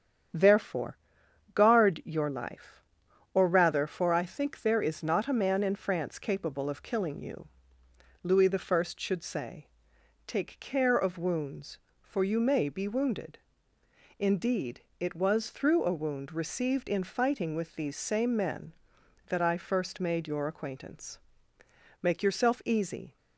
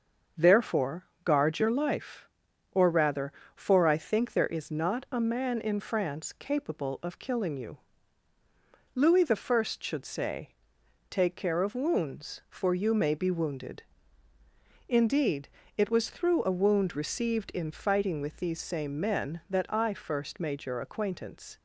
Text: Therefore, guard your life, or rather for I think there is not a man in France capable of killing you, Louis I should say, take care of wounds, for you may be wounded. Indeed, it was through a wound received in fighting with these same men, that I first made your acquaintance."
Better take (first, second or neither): second